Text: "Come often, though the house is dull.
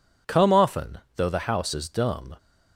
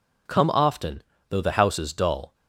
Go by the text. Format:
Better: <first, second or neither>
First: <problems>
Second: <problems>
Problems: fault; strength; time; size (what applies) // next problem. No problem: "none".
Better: second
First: says "dumb" for "dull"; at 1.8 s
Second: none